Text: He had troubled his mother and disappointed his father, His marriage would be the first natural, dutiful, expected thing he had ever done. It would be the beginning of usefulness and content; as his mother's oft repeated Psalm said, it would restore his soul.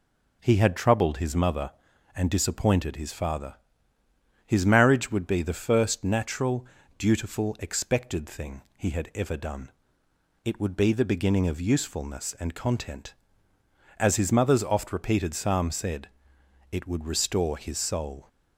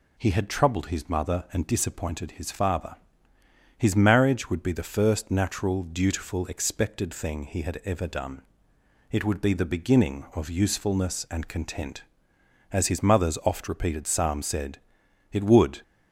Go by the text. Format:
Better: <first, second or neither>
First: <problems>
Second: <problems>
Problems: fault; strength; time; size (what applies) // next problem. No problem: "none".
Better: first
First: none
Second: stops before "restore his soul"; at 15.8 s